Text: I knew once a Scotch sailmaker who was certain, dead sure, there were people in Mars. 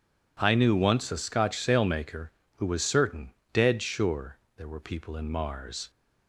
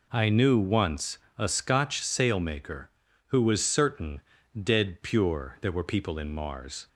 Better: first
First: none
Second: pauses between "once" and "a"; slight; at 1.1 s; 0.20 s long // says "pure" for "sure"; at 5.0 s

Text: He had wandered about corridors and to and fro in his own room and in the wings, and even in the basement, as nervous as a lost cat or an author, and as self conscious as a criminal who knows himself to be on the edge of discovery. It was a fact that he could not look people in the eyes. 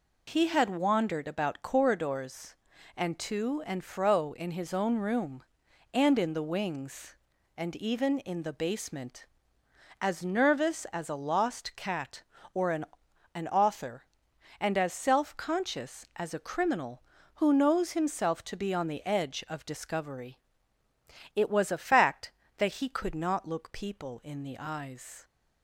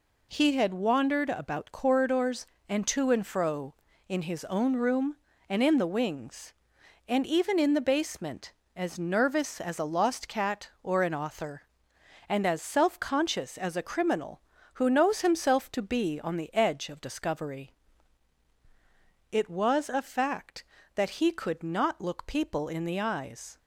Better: second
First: says "an" twice; at 13.3 s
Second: none

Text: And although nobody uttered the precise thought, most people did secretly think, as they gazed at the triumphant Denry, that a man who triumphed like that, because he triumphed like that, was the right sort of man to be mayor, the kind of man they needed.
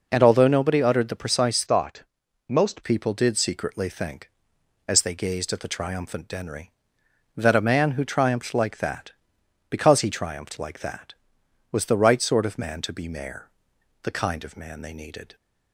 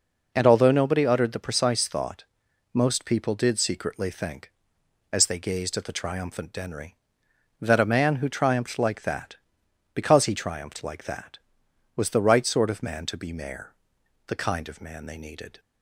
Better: second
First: changes voice from "thought" to "most"; from 1.6 to 2.8 s; 1.2 s long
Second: none

